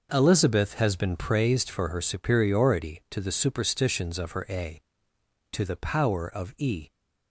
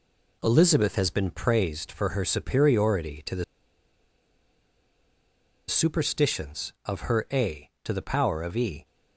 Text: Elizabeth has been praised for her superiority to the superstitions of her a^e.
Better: first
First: none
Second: pauses between "the" and "superstitions"; strong; at 3.4 s; 2.2 s long

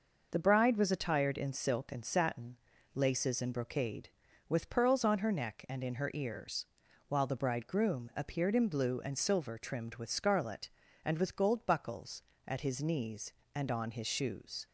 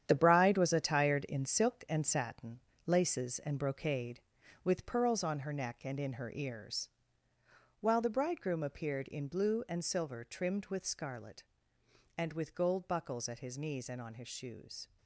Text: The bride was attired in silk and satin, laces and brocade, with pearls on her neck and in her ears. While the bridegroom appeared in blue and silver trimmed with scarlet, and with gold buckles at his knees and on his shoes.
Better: first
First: none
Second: gets quieter; strong; throughout; 9.5 dB

